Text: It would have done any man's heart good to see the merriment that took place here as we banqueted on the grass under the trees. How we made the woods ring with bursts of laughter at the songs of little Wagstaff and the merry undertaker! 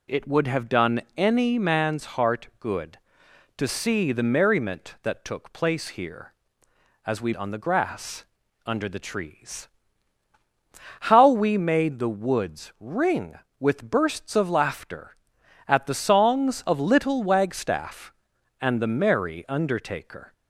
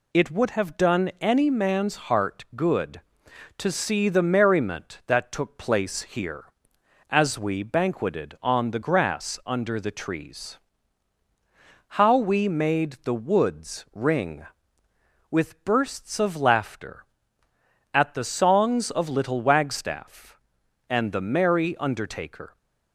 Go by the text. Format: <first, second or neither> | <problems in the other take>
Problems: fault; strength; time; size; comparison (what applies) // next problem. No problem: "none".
second | skips "banqueted"; at 7.3 s // pauses between "grass" and "under"; at 8.2 s; 0.40 s long